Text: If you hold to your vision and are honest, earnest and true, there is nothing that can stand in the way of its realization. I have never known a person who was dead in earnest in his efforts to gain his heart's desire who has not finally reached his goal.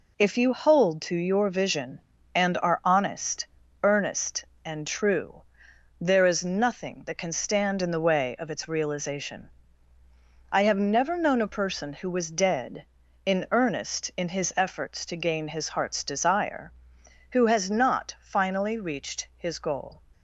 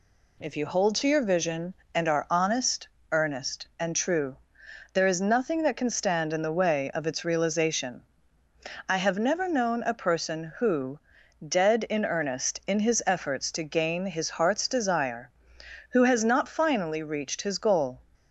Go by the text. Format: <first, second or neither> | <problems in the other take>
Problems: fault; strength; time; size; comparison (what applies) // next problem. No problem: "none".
first | skips "was"; at 11.2 s